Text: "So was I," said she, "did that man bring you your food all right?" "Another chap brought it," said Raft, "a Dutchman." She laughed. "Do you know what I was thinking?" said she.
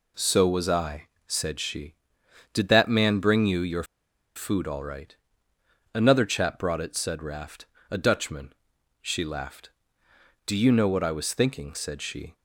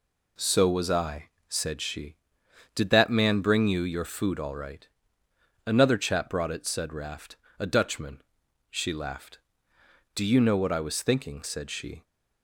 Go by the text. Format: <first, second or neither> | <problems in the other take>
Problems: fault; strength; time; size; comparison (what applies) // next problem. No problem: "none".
second | pauses between "your" and "food"; noticeable; at 3.8 s; 0.52 s long